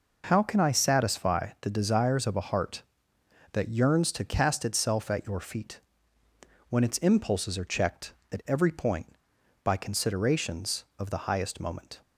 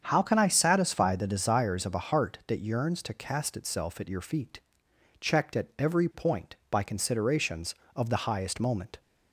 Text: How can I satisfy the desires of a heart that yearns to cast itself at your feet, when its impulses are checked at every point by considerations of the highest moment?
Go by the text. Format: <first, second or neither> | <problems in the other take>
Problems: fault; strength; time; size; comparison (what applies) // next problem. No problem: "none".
first | starts louder than the rest; strong; until 1.0 s; 7.5 dB // skips "when its impulses are"; at 4.9 s